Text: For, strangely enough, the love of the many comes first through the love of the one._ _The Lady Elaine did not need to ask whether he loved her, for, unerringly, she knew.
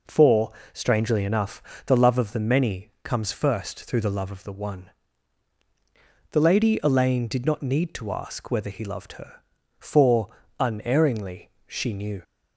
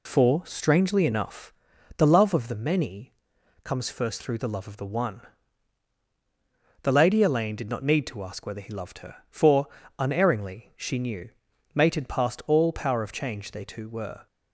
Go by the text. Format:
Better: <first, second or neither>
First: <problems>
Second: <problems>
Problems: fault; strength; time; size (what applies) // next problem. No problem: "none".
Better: first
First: none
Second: pauses between "many" and "comes"; noticeable; at 3.1 s; 0.52 s long // goes on to say "Mated past all power of change they two were"; strong; from 11.7 s on; 2.5 s long